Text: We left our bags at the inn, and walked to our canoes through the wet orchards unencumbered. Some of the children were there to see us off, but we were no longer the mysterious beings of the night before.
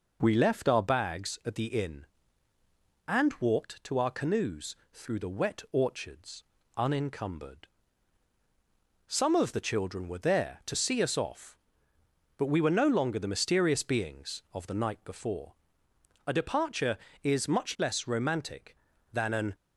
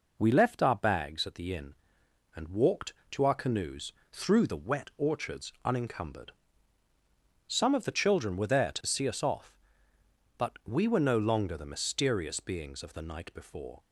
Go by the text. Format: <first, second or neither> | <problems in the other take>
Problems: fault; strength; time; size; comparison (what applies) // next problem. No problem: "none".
second | pauses between "canoes" and "through"; slight; at 4.7 s; 0.18 s long; slight in the second // pauses between "orchards" and "unencumbered"; slight; at 6.4 s; 0.34 s long // goes on to say "A departure is much less romantic than an"; strong; from 16.2 s on; 3.2 s long